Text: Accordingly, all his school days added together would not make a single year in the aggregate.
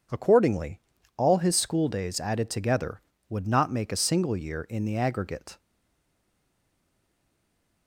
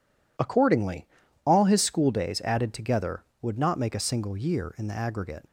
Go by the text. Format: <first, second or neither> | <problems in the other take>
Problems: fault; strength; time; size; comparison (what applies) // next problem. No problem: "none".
second | stays silent after the last word; from 5.5 s on; 2.3 s long